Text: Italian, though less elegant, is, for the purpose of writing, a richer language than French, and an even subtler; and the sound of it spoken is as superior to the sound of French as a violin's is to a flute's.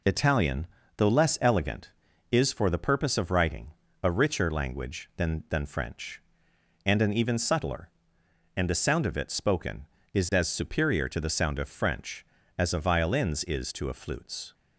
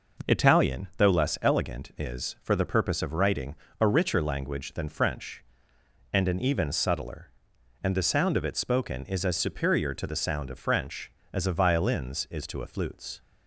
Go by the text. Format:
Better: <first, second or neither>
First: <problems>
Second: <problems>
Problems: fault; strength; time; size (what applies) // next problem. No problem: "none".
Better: second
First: says "than" twice; at 5.4 s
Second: none